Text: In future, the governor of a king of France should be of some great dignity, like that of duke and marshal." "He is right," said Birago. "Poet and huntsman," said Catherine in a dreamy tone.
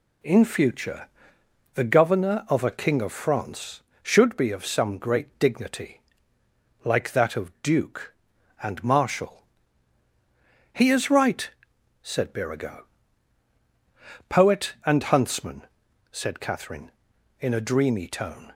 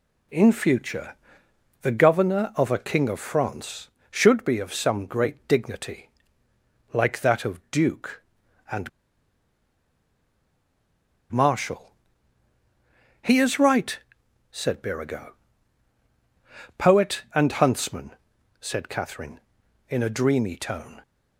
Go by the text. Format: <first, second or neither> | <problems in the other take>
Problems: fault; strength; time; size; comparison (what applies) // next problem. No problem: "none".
first | pauses between "and" and "marshal"; strong; at 8.8 s; 2.4 s long